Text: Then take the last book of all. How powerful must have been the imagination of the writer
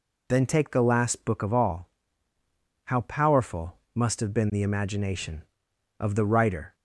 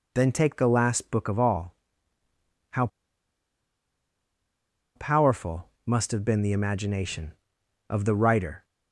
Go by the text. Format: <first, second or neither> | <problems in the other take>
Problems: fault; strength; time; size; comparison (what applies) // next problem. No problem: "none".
first | pauses between "How" and "powerful"; strong; at 2.8 s; 2.0 s long // pauses between "powerful" and "must"; slight; at 5.6 s; 0.16 s long; slight in the first